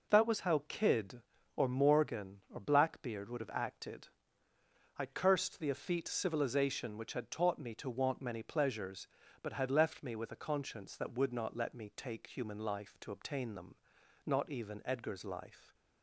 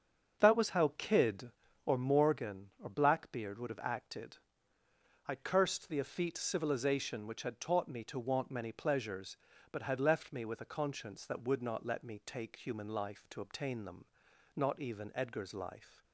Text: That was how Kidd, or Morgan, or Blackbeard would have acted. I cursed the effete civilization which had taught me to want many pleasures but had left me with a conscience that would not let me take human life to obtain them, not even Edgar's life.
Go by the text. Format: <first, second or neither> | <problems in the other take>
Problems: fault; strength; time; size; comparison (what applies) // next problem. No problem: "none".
first | starts louder than the rest; until 2.0 s; 6.5 dB